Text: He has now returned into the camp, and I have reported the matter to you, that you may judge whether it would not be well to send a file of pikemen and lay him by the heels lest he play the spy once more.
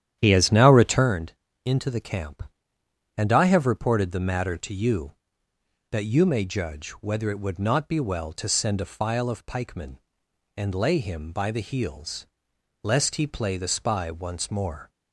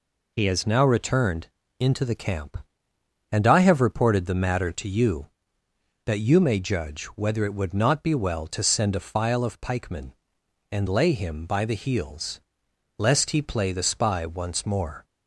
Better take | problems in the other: second | starts louder than the rest; strong; until 1.1 s; 10 dB // pauses between "returned" and "into"; slight; at 1.3 s; 0.30 s long; slight in the second // pauses between "heels" and "lest"; noticeable; at 12.2 s; 0.56 s long; noticeable in the second

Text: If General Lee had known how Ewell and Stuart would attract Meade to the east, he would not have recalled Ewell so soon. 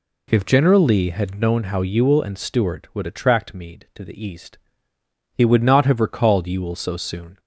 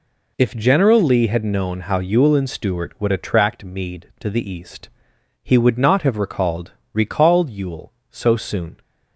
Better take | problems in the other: first | says "recalled" twice; at 6.9 s

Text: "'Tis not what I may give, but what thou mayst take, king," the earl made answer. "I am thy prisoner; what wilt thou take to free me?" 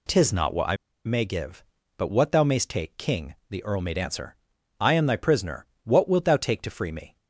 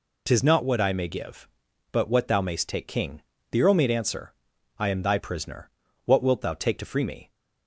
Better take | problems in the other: second | pauses between "I" and "may"; slight; at 0.7 s; 0.29 s long

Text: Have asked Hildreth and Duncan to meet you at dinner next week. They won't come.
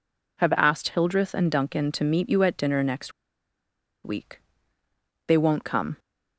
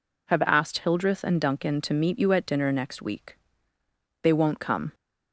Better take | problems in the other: second | pauses between "next" and "week"; noticeable; at 3.1 s; 0.92 s long

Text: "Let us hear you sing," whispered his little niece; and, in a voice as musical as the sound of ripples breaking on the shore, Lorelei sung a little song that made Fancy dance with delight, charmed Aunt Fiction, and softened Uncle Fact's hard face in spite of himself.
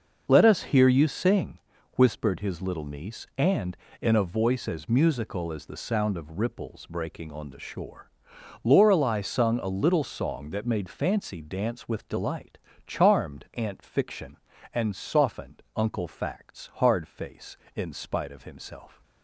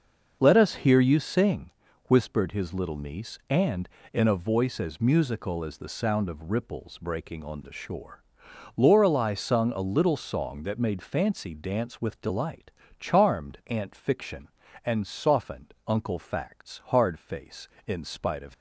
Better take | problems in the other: first | pauses between "softened" and "Uncle"; slight; at 15.7 s; 0.16 s long; slight in the first // stops before "himself"; at 18.5 s

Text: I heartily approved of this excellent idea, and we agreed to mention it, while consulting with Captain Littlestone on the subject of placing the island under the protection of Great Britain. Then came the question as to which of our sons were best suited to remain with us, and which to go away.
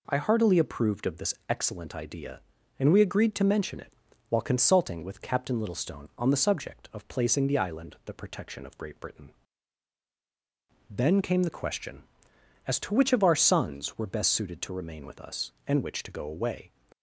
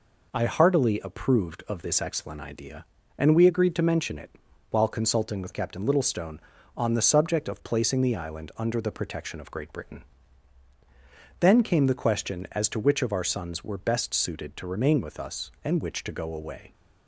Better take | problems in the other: second | pauses between "this" and "excellent"; slight; at 1.3 s; 0.16 s long // skips "under"; at 7.9 s

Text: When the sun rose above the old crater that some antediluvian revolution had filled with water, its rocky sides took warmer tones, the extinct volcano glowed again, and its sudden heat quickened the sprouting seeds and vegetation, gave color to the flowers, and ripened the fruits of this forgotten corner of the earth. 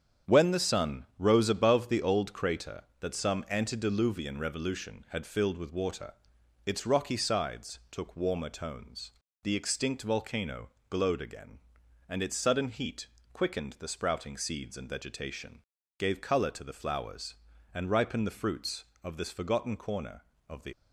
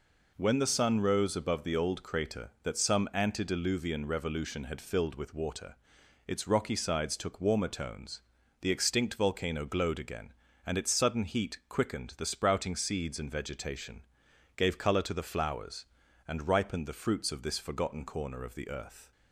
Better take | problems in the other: second | starts louder than the rest; strong; until 1.4 s; 8.5 dB // pauses between "volcano" and "glowed"; slight; at 10.6 s; 0.20 s long // pauses between "heat" and "quickened"; slight; at 13.0 s; 0.28 s long // stops before "earth"; at 20.7 s

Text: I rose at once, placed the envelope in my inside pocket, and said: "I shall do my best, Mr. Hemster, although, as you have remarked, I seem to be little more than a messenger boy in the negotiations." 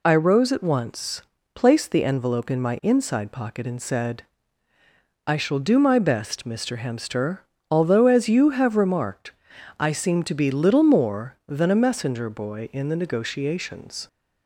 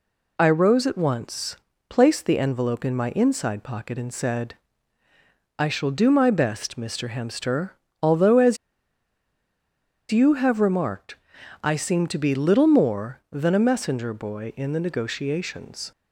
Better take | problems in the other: first | pauses between "as" and "you"; strong; at 8.5 s; 1.5 s long

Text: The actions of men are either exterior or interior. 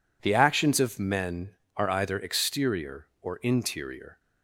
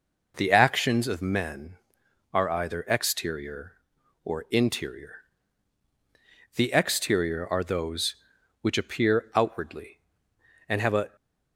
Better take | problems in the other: first | goes on to say "The exterior are those which appear outwardly and have a"; strong; from 6.5 s on; 4.6 s long

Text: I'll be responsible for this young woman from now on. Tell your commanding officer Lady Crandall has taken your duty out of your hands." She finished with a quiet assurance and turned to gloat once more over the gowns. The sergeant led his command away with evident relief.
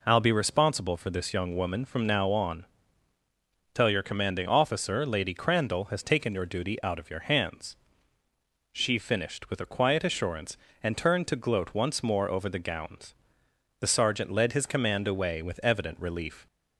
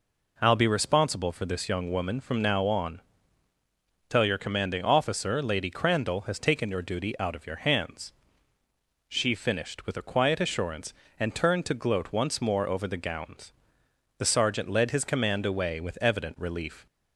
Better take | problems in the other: neither | none

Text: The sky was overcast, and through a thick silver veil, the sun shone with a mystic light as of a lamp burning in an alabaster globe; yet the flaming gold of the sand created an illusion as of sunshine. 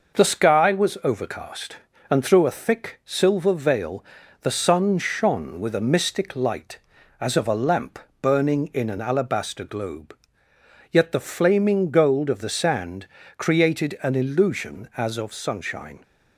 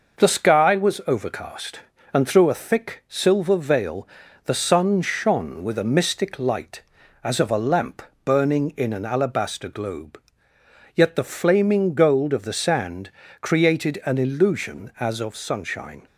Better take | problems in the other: neither | pauses between "lamp" and "burning"; slight; the same in both // pauses between "sand" and "created"; slight; the same in both

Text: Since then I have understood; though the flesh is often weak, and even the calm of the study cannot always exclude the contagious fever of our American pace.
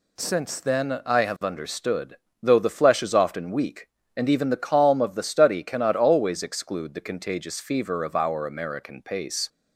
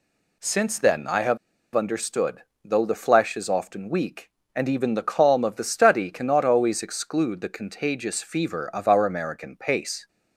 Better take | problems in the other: first | pauses between "have" and "understood"; at 1.3 s; 0.37 s long

